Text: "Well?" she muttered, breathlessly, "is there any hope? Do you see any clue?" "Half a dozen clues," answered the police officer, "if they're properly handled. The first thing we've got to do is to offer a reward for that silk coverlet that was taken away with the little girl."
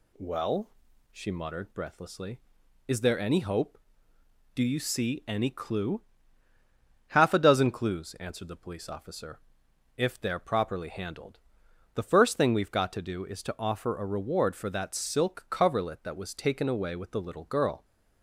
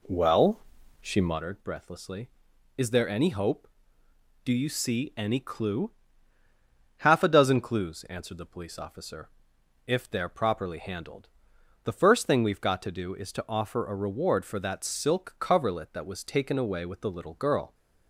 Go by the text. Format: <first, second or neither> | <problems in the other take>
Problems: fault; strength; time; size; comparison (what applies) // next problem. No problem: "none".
first | starts louder than the rest; slight; until 1.4 s; 3 dB